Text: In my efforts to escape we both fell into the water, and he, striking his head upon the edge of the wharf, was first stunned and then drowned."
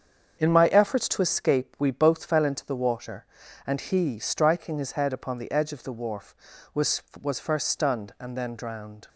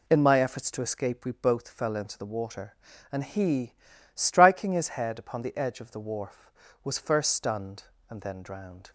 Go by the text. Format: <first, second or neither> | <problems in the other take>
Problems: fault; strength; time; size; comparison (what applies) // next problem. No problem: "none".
second | starts louder than the rest; until 1.4 s; 7 dB // says "was" twice; at 7.1 s